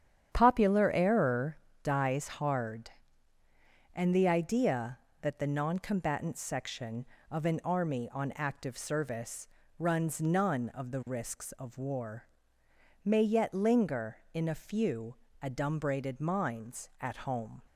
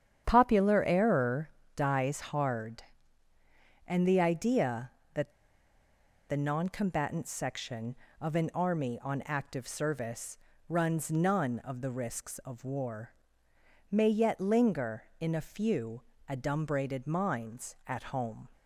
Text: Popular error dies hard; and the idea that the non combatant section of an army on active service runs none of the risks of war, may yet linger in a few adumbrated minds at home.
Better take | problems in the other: first | starts louder than the rest; strong; until 1.2 s; 9 dB; strong in the first // pauses between "error" and "dies"; slight; at 1.5 s; 0.24 s long; slight in the first // pauses between "that" and "the"; at 5.2 s; 1.0 s long // pauses between "service" and "runs"; slight; at 10.3 s; 0.30 s long; slight in the first // pauses between "few" and "adumbrated"; slight; at 16.0 s; 0.26 s long; slight in the first

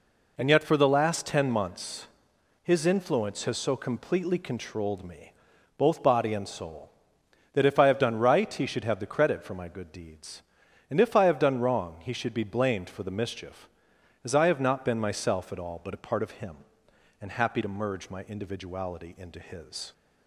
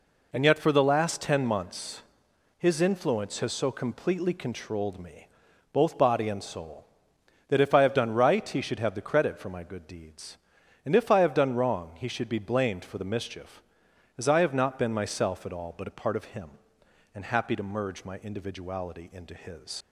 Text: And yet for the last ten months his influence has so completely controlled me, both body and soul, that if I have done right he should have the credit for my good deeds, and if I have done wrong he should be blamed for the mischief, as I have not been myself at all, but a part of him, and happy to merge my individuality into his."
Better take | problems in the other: first | pauses between "months" and "his"; noticeable; at 2.0 s; 0.54 s long; noticeable in the first // leaves "his" unfinished; at 19.8 s; 65 ms

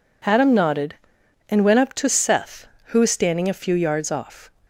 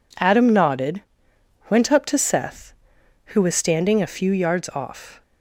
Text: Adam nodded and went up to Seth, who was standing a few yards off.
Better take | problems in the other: first | skips "and"; at 1.3 s

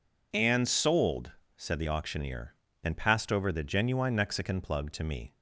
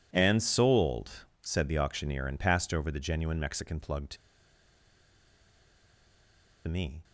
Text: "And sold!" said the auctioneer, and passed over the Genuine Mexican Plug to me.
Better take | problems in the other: first | pauses between "to" and "me"; strong; at 4.1 s; 2.5 s long

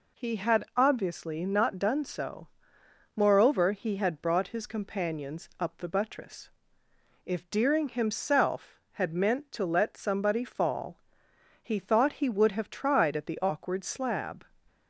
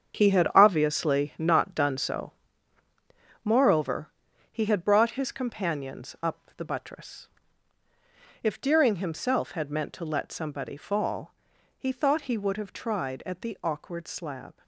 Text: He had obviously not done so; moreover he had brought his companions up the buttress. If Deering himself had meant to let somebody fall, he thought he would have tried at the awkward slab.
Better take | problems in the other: first | gets quieter; strong; throughout; 10 dB // pauses between "moreover" and "he"; at 4.0 s; 0.42 s long

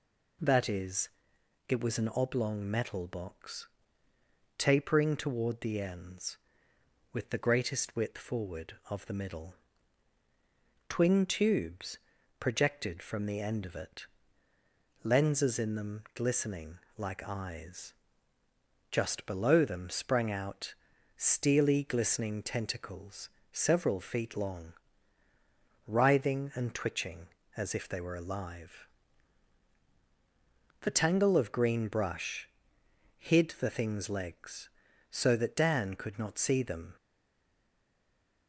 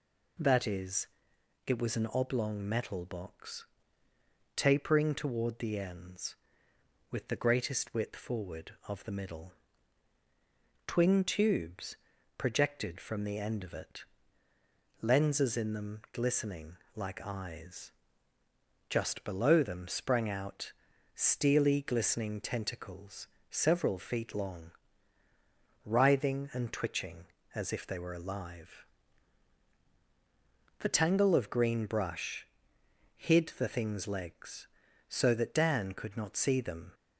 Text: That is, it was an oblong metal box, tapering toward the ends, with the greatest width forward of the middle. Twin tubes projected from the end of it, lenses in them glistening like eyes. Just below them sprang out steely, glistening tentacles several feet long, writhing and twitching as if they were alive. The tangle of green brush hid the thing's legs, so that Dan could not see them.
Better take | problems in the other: second | pauses between "tubes" and "projected"; at 11.9 s; 0.40 s long; also in the second // pauses between "glistening" and "like"; slight; at 16.7 s; 0.18 s long; slight in the second // pauses between "out" and "steely"; at 20.7 s; 0.44 s long; also in the second // pauses between "tentacles" and "several"; slight; at 23.2 s; 0.24 s long; slight in the second // pauses between "brush" and "hid"; noticeable; at 32.4 s; 0.70 s long; noticeable in the second // stays silent after the last word; noticeable; from 36.9 s on; 1.5 s long

